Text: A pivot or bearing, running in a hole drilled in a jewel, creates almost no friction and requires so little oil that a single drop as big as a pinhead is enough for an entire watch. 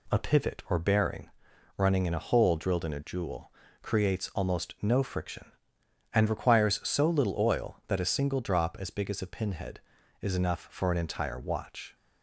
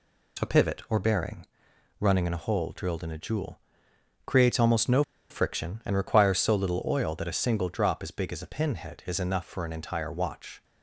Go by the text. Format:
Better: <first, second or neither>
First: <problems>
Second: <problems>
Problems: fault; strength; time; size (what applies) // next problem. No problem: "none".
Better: first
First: none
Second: pauses between "no" and "friction"; slight; at 5.0 s; 0.28 s long